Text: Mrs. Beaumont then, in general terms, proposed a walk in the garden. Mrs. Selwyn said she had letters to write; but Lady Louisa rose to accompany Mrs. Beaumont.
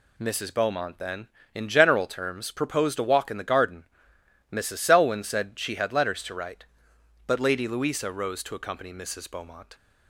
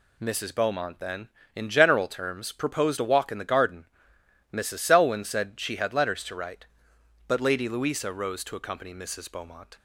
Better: neither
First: none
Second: none

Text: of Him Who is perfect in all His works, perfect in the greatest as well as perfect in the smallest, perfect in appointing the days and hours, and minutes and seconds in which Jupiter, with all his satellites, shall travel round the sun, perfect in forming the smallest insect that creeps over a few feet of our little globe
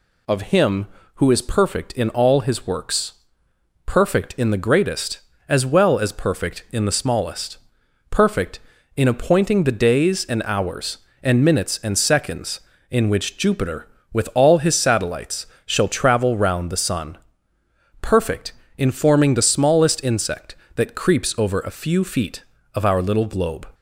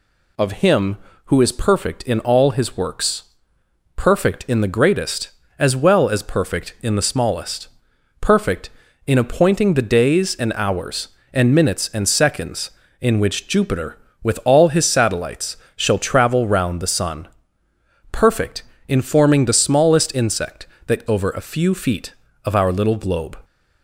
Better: first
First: none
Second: skips "creeps"; at 21.0 s

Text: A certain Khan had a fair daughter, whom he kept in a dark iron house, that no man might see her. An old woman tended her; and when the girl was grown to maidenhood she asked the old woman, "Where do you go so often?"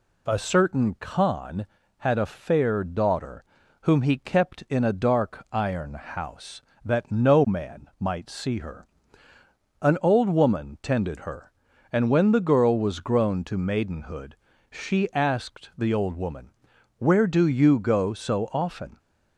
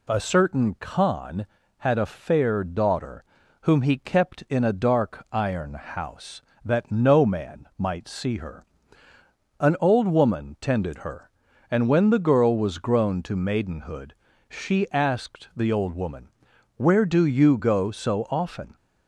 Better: neither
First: pauses between "maidenhood" and "she"; slight; at 14.3 s; 0.34 s long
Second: pauses between "maidenhood" and "she"; slight; at 14.1 s; 0.34 s long

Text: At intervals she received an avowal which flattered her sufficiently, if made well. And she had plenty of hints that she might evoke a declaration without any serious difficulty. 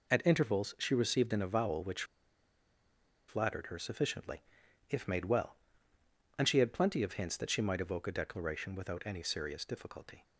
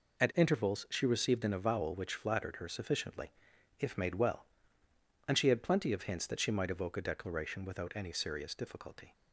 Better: second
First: pauses between "which" and "flattered"; strong; at 2.0 s; 1.2 s long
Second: none

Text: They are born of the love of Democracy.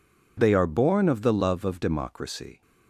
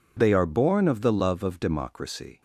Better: neither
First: none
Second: none

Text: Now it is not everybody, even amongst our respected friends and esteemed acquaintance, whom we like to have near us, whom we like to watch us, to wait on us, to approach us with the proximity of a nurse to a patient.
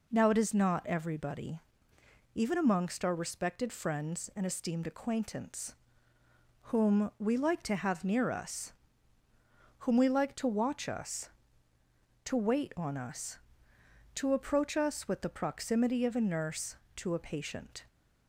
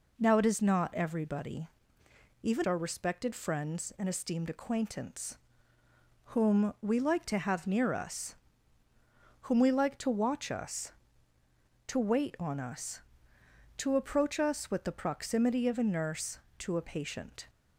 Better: first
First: none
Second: skips "amongst"; at 2.6 s

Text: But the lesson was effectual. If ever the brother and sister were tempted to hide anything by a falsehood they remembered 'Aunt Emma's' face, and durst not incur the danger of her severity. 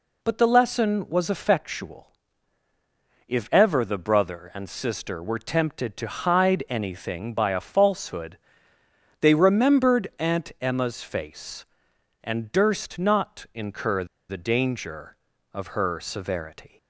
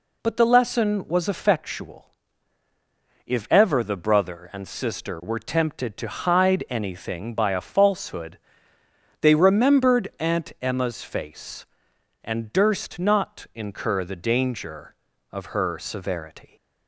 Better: second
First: pauses between "falsehood" and "they"; noticeable; at 8.3 s; 0.84 s long // pauses between "incur" and "the"; slight; at 14.0 s; 0.24 s long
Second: pauses between "falsehood" and "they"; noticeable; at 8.3 s; 0.84 s long

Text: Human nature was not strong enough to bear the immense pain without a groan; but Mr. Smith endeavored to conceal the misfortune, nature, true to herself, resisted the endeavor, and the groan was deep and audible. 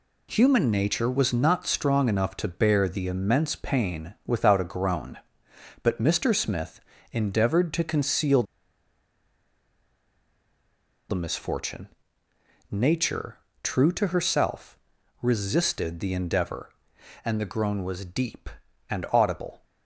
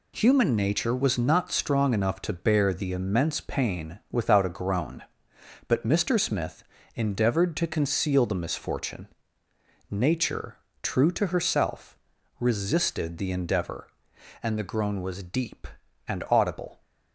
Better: second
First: pauses between "Smith" and "endeavored"; slight; at 6.7 s; 0.32 s long // pauses between "conceal" and "the"; strong; at 8.4 s; 2.6 s long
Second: pauses between "Smith" and "endeavored"; slight; at 6.6 s; 0.32 s long

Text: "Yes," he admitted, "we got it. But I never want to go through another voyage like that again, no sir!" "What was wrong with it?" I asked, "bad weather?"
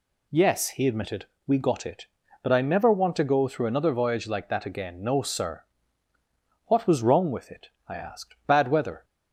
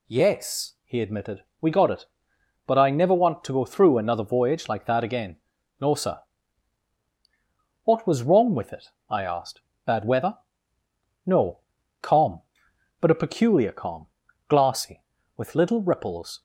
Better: first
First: none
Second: goes on to say "No calm but a peculiar calm glassy with little ripples"; strong; from 11.2 s on; 5.1 s long

